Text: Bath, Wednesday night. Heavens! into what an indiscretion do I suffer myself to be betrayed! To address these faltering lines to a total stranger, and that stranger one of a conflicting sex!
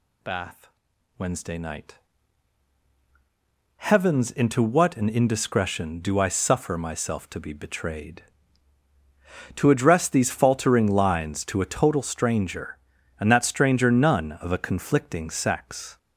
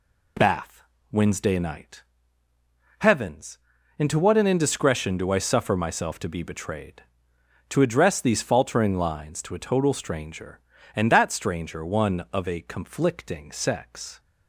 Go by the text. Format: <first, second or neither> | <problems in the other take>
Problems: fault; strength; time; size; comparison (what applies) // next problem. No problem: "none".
second | says "none" for "one"; at 13.8 s